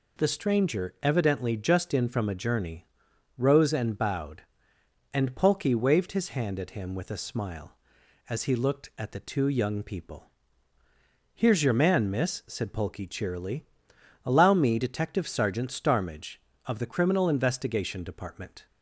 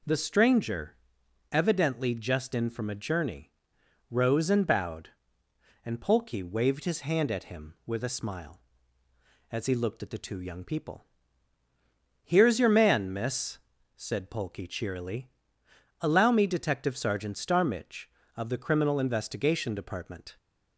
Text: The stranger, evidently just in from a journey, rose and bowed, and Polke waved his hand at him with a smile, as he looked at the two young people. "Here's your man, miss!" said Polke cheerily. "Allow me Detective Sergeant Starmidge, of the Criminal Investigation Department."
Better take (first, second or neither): neither